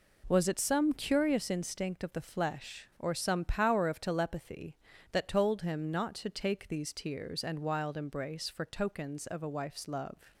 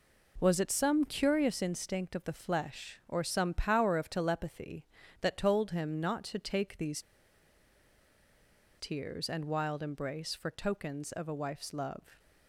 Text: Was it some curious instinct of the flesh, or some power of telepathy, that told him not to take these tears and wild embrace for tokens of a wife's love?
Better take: first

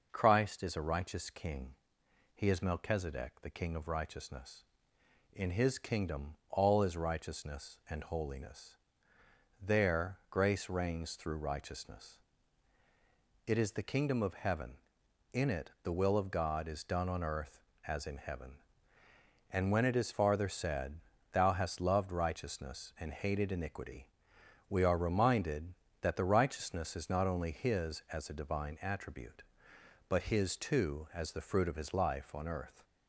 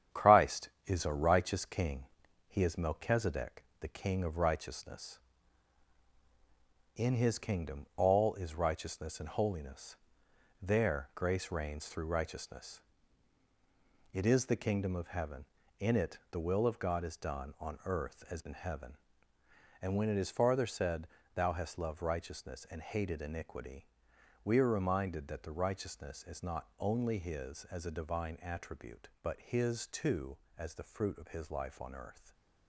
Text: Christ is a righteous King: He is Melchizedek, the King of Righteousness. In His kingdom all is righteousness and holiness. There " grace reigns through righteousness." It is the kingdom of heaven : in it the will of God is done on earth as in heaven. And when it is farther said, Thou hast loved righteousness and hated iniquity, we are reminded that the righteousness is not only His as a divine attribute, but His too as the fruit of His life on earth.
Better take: first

